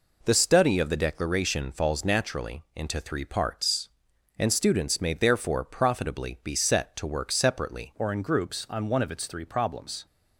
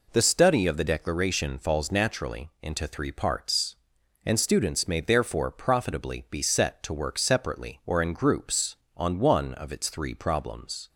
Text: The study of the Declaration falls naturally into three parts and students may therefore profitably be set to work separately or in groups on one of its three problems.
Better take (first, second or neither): second